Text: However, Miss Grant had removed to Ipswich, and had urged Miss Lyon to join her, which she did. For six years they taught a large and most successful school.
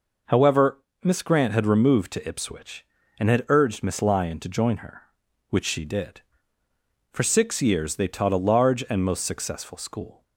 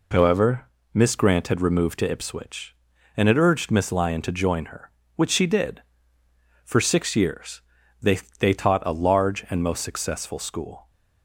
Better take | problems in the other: first | pauses between "years" and "they"; at 7.6 s; 0.40 s long // says "they" twice; at 8.3 s

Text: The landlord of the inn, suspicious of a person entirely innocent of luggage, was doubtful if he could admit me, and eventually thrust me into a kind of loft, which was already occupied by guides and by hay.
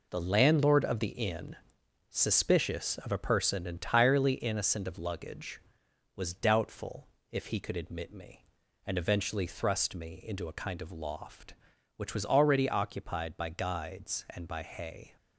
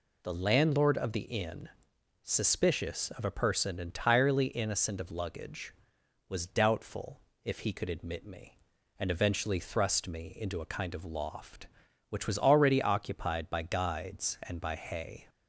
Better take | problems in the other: second | gets quieter; strong; throughout; 7.5 dB // pauses between "doubtful" and "if"; slight; at 7.0 s; 0.22 s long; slight in the second

